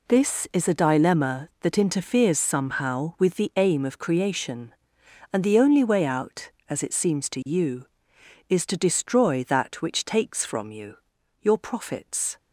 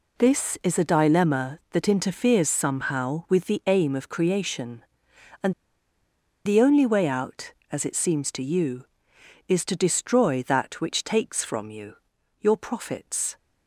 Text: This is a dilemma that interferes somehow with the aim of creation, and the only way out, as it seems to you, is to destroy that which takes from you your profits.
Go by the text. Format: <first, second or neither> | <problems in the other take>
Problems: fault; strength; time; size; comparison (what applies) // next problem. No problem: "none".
first | pauses between "and" and "the"; noticeable; at 5.5 s; 0.93 s long // pauses between "you" and "your"; noticeable; at 11.9 s; 0.46 s long; noticeable in the first